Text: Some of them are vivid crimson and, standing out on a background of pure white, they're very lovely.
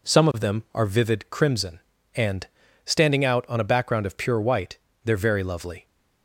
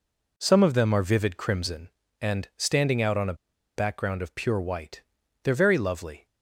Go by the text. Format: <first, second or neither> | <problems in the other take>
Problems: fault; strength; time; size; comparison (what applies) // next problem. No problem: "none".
first | pauses between "a" and "background"; at 3.3 s; 0.42 s long